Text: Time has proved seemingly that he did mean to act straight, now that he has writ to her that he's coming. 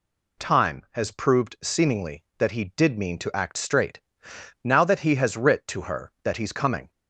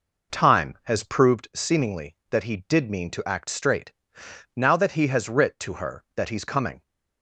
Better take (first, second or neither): first